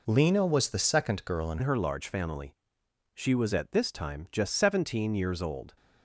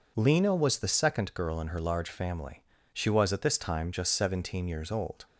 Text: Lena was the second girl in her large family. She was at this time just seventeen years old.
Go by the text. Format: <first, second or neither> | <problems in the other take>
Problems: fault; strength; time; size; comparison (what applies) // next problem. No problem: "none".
second | changes voice at "her"; from 1.6 s on; 4.1 s long